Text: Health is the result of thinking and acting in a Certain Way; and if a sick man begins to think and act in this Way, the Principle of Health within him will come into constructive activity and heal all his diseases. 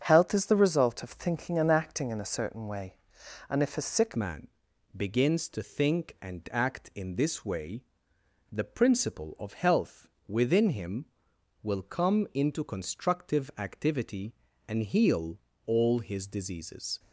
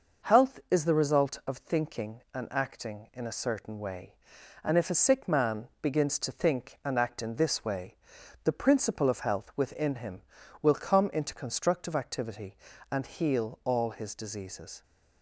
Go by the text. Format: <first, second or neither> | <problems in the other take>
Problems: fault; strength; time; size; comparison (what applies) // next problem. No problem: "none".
second | starts louder than the rest; strong; until 1.0 s; 7 dB // changes voice at "man"; from 4.1 s on; 12.8 s long // pauses between "man" and "begins"; noticeable; at 4.4 s; 0.46 s long // pauses between "Health" and "within"; slight; at 10.0 s; 0.20 s long // pauses between "heal" and "all"; slight; at 15.3 s; 0.26 s long